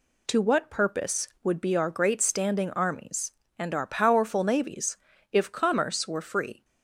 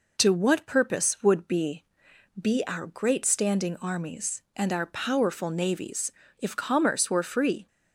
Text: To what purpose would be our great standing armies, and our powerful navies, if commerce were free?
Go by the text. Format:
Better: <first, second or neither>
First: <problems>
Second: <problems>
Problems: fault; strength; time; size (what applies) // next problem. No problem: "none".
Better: first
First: none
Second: says "be" twice; at 2.3 s